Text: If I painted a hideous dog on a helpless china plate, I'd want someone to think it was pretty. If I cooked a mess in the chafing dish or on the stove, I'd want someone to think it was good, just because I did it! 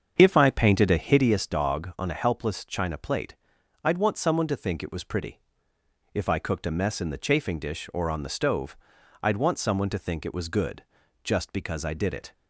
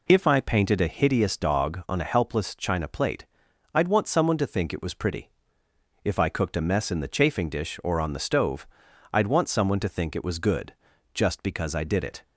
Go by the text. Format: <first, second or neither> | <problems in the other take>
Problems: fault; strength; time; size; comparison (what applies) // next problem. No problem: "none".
second | starts louder than the rest; strong; until 1.5 s; 7.5 dB